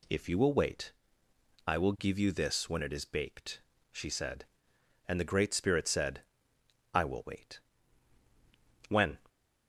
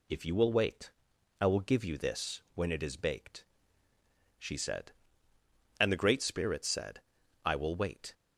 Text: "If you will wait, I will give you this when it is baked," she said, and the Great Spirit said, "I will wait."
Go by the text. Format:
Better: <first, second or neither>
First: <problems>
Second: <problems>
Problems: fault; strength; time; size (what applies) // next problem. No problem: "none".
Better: second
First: goes on to say "When"; slight; from 8.8 s on; 0.30 s long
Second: none